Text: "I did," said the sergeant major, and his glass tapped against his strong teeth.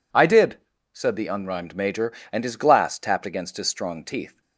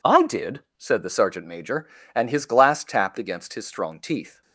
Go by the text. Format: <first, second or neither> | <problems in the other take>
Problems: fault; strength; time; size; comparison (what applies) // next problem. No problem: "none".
second | says "unrhymed" for "sergeant"; at 1.2 s